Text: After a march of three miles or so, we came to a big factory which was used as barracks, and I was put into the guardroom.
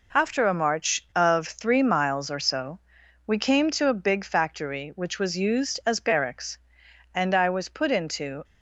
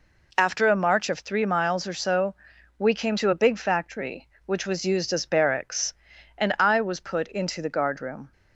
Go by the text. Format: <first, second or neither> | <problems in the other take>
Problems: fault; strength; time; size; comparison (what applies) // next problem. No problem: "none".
second | stops before "the guardroom"; at 8.4 s